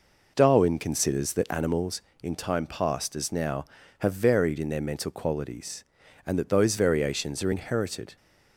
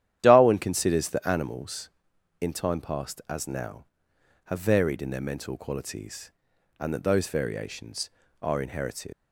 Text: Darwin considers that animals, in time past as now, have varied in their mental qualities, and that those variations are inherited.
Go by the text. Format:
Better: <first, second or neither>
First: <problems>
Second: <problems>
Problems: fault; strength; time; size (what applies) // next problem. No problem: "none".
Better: first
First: none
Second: starts louder than the rest; strong; until 1.2 s; 11 dB // leaves "inherited" unfinished; at 9.1 s; 95 ms